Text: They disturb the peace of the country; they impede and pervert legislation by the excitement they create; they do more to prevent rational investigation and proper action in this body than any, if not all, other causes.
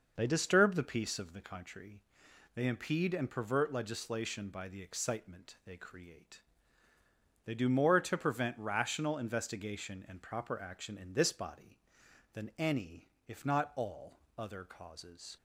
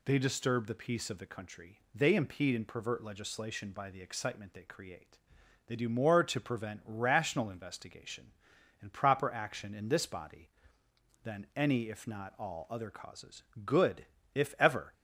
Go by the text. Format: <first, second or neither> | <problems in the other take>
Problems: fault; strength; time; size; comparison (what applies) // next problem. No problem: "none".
first | goes on to say "Good if ever"; noticeable; from 13.6 s on; 1.2 s long